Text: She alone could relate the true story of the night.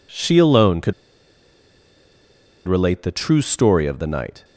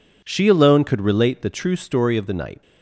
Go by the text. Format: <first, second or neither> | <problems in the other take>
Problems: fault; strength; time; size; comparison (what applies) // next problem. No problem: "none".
second | pauses between "could" and "relate"; strong; at 0.9 s; 1.7 s long